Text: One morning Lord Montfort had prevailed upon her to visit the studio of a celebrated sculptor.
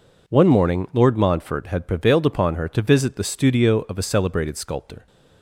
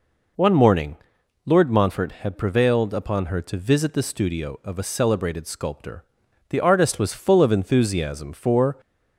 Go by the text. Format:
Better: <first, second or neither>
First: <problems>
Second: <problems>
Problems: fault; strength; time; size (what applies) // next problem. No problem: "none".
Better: first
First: none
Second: pauses between "morning" and "Lord"; noticeable; at 0.9 s; 0.48 s long // goes on to say "The artist was full of enthusiasm for"; strong; from 6.4 s on; 2.2 s long